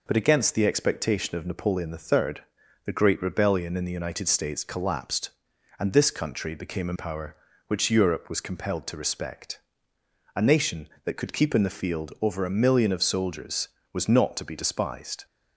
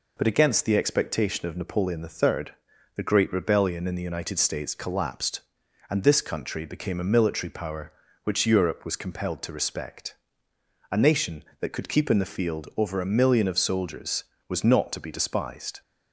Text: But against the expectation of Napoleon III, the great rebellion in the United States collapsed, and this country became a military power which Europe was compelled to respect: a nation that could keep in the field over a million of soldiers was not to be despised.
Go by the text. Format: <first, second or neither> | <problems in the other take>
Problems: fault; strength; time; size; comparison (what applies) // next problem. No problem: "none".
second | skips "military"; at 6.9 s